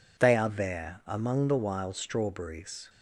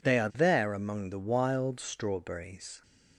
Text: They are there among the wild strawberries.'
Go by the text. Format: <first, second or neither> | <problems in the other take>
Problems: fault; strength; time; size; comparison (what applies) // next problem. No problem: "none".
neither | none